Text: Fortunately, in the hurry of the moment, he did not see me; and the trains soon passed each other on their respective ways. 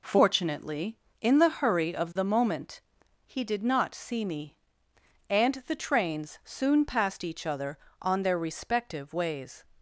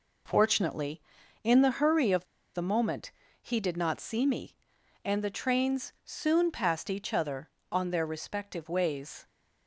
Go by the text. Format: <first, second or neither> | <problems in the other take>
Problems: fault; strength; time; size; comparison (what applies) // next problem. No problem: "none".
first | pauses between "of" and "the"; slight; at 2.2 s; 0.29 s long